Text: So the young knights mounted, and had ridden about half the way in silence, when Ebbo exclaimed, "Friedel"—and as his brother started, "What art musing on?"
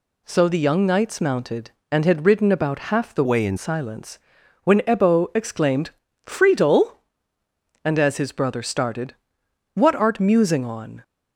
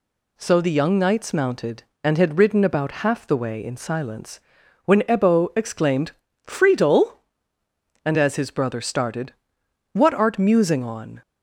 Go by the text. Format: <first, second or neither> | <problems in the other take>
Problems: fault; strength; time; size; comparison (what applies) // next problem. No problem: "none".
second | changes voice from "way" to "in"; from 3.2 to 3.5 s; 0.3 s long